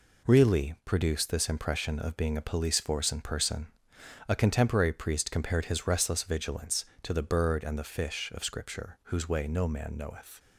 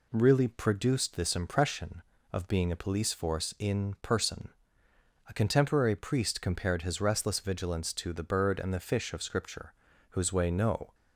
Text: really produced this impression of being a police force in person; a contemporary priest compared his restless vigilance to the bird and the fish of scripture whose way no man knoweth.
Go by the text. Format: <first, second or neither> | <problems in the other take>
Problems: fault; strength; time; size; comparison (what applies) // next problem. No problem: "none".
first | pauses between "scripture" and "whose"; at 9.7 s; 0.38 s long // stops before "man knoweth"; at 10.9 s